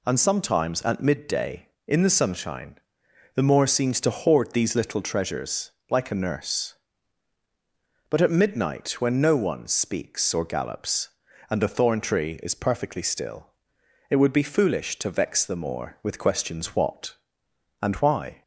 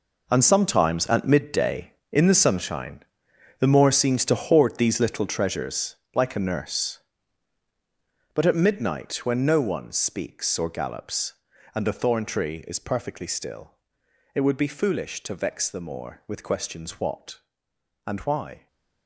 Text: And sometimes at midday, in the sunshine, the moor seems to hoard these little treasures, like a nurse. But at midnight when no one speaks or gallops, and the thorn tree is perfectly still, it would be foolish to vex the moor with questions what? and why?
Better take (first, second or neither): first